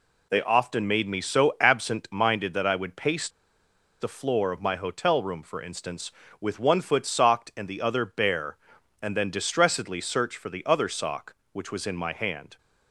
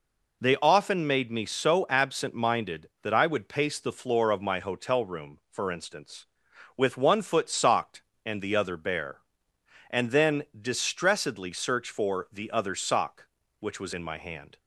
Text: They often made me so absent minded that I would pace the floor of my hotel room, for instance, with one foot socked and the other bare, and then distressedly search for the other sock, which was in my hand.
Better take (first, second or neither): second